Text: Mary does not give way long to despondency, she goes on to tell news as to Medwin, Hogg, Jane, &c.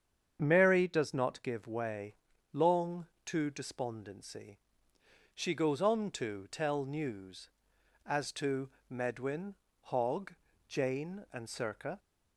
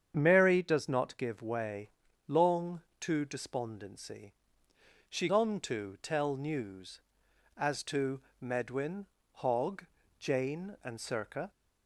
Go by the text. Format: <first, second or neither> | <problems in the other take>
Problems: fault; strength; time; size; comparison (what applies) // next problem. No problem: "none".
first | starts louder than the rest; strong; until 1.1 s; 8 dB; strong in the first // pauses between "way" and "long"; slight; at 1.8 s; 0.36 s long; slight in the first // skips "goes"; at 5.2 s // pauses between "to" and "Medwin"; slight; at 8.1 s; 0.20 s long; slight in the first